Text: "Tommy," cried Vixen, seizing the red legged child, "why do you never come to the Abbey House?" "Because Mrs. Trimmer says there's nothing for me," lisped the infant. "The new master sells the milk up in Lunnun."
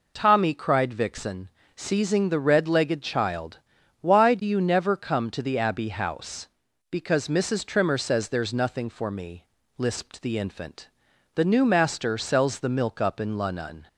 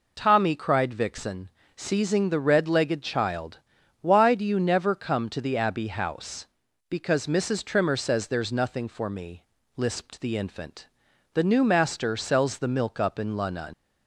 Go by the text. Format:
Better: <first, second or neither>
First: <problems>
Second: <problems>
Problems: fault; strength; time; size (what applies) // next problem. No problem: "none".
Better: first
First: none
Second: leaves "Lunnun" unfinished; at 13.7 s; 125 ms